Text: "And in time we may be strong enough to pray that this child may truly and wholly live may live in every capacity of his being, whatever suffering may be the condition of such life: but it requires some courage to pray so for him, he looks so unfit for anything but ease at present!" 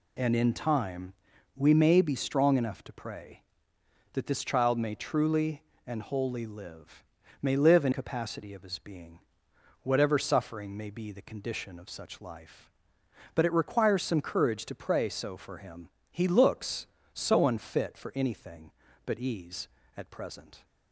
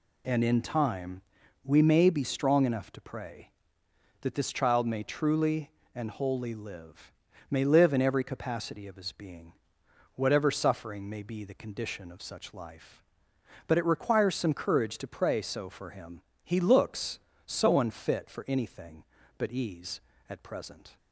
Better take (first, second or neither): second